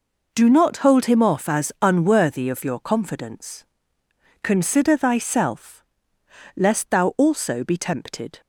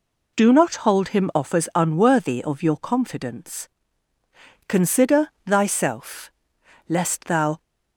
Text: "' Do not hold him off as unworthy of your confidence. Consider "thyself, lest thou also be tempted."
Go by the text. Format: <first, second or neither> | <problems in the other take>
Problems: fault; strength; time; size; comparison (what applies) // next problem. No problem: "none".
first | pauses between "Consider" and "thyself"; slight; at 5.2 s; 0.18 s long // stops before "also be tempted"; at 7.6 s